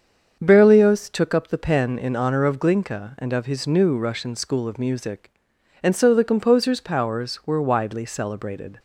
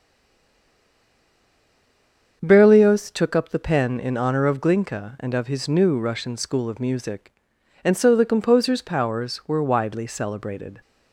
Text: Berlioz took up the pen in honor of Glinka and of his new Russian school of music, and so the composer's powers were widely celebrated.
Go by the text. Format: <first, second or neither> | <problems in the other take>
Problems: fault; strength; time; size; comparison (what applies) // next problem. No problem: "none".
first | stays silent before the first word; until 2.4 s; 2.4 s long // starts louder than the rest; until 3.4 s; 7 dB; also in the first